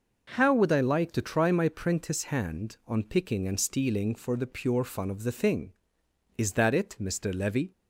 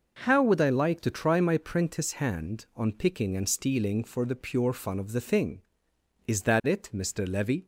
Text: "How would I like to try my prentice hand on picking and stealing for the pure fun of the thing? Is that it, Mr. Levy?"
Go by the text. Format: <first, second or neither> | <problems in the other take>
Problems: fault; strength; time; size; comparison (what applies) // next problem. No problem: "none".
neither | none